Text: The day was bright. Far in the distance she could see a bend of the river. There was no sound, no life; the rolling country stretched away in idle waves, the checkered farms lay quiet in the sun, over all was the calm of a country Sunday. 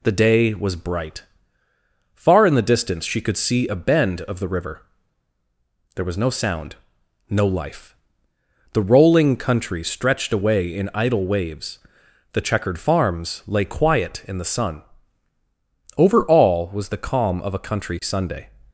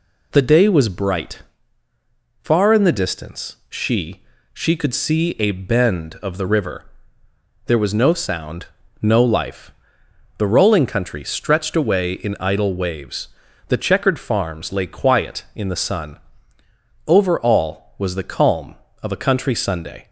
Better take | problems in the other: first | says "she" twice; at 4.5 s

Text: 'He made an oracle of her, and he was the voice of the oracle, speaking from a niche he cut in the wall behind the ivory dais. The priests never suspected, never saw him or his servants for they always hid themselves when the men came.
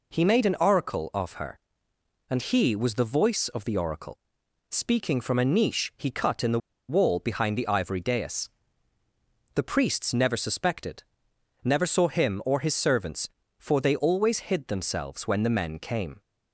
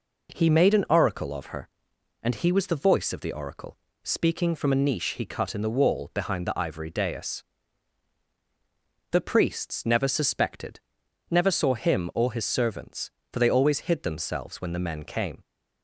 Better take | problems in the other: second | pauses between "the" and "wall"; slight; at 6.5 s; 0.28 s long

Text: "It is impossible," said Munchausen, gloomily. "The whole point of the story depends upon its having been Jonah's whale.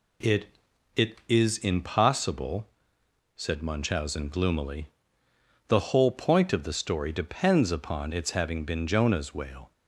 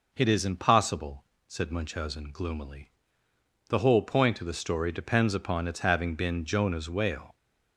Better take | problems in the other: second | says "It" twice; at 0.9 s

